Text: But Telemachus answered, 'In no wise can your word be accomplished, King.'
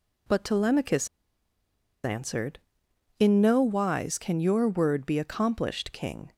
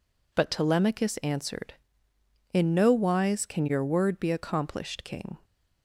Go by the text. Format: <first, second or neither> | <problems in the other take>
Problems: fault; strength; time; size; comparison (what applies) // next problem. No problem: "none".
second | pauses between "Telemachus" and "answered"; noticeable; at 1.0 s; 0.96 s long